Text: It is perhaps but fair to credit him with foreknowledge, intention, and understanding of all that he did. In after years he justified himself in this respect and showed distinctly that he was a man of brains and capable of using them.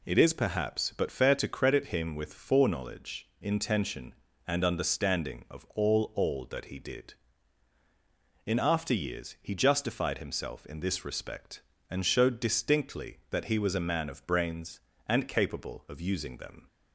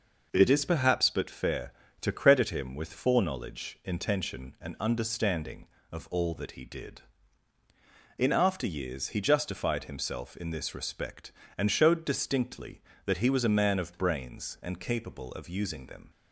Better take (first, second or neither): second